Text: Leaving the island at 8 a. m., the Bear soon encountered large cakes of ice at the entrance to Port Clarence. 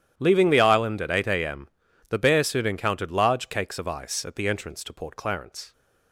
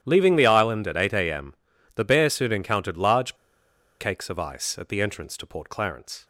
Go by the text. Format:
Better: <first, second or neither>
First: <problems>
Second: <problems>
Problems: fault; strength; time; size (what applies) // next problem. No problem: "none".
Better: first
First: starts louder than the rest; strong; until 1.1 s; 10.5 dB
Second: starts louder than the rest; strong; until 1.0 s; 11 dB // pauses between "large" and "cakes"; noticeable; at 3.3 s; 0.64 s long